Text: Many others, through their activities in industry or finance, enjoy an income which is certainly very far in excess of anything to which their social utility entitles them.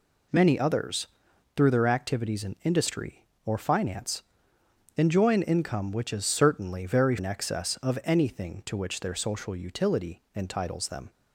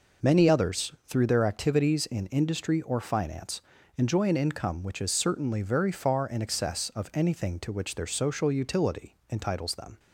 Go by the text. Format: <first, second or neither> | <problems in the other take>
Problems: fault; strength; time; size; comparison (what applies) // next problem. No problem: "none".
second | skips "far"; at 7.1 s